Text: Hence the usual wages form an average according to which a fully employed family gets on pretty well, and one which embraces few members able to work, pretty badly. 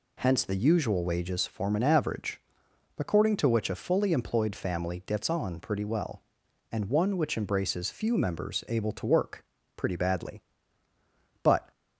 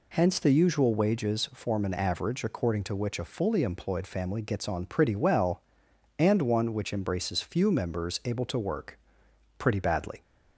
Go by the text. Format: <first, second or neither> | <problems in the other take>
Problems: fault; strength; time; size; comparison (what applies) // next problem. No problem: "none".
second | pauses between "average" and "according"; noticeable; at 2.4 s; 0.60 s long // goes on to say "But"; slight; from 11.4 s on; 0.26 s long